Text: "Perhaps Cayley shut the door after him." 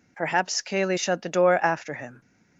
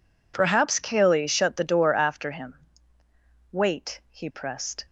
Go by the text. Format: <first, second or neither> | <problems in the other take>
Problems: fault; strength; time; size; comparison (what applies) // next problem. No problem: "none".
first | goes on to say "Wait He pressed"; from 3.5 s on; 1.3 s long